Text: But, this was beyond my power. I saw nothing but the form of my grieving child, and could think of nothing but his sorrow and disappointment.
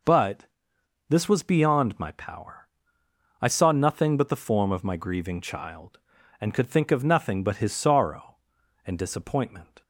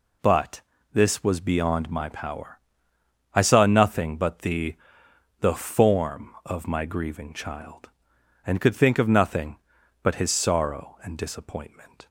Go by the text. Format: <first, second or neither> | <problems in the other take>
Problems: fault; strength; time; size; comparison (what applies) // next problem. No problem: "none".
first | says "the" twice; at 5.3 s